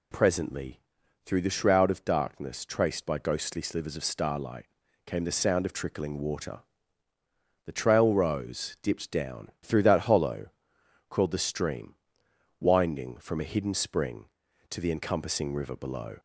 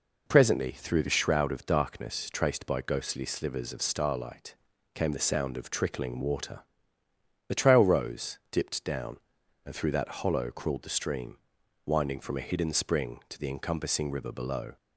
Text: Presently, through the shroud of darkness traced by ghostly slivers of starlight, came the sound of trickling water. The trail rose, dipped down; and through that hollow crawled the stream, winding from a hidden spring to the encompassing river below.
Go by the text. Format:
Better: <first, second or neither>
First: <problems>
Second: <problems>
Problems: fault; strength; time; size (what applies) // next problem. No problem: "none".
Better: second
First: skips "and"; at 9.5 s // pauses between "hollow" and "crawled"; noticeable; at 10.4 s; 0.62 s long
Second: none